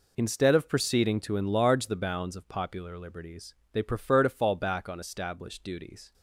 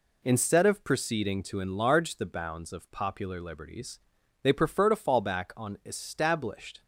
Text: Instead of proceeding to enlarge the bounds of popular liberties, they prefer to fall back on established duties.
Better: first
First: none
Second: stops before "duties"; at 6.8 s

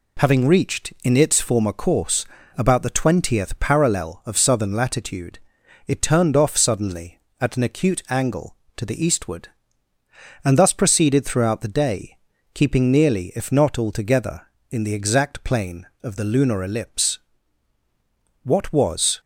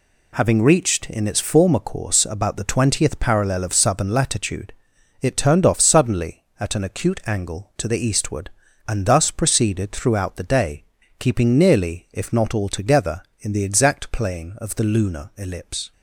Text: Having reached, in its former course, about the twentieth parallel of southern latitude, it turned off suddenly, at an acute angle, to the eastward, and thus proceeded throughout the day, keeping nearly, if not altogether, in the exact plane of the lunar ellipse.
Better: second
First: goes on to say "What was"; noticeable; from 18.4 s on; 0.78 s long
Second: none

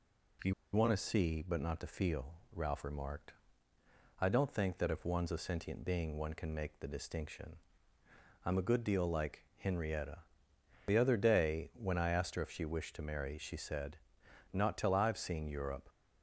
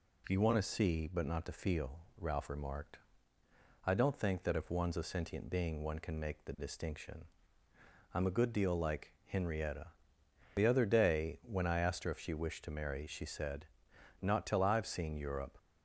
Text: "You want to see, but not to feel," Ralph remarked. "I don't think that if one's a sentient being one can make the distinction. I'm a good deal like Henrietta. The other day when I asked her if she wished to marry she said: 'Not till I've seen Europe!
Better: second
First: pauses between "You" and "want"; slight; at 0.5 s; 0.22 s long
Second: none

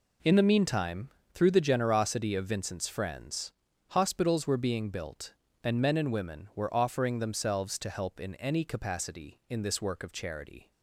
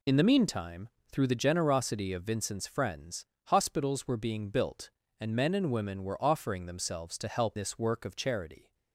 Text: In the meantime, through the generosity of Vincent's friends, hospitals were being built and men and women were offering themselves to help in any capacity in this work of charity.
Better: first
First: none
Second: skips "in any capacity in"; at 7.5 s

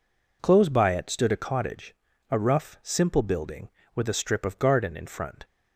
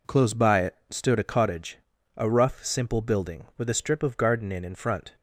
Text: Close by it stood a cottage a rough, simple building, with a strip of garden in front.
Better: first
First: pauses between "cottage" and "a"; slight; at 1.9 s; 0.36 s long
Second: pauses between "cottage" and "a"; at 1.7 s; 0.38 s long // says "in" twice; at 4.6 s

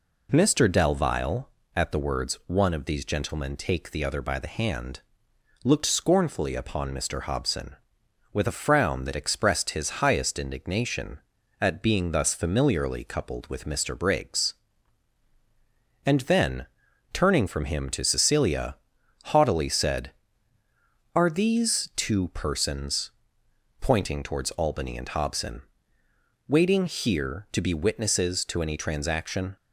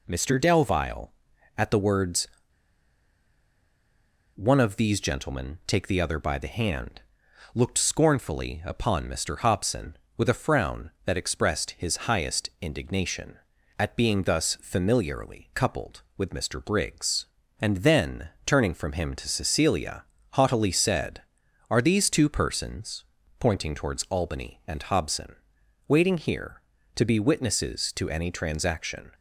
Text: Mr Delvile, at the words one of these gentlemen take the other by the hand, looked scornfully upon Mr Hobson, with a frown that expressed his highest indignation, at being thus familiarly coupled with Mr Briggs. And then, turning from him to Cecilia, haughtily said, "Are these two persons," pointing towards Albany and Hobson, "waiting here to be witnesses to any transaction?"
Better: first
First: none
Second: pauses between "words" and "one"; strong; at 2.2 s; 2.0 s long

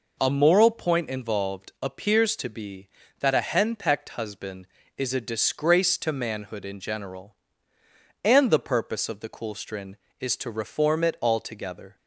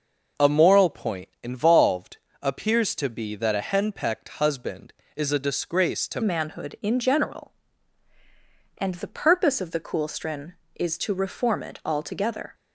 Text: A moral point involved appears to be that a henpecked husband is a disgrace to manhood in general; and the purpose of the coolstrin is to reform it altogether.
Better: first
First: none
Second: pauses between "involved" and "appears"; slight; at 2.1 s; 0.24 s long // changes voice at "manhood"; from 6.2 s on; 6.3 s long

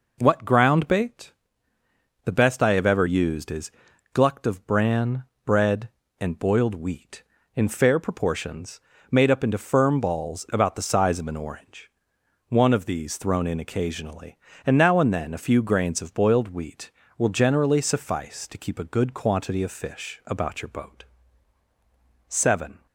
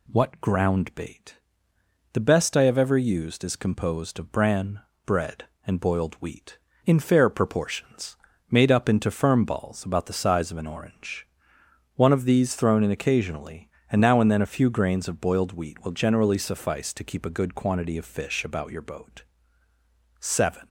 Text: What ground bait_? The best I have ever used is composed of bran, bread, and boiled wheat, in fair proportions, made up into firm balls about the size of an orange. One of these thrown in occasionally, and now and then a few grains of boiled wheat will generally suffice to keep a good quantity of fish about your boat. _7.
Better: second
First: says "glucked" for "composed"; at 4.1 s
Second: none

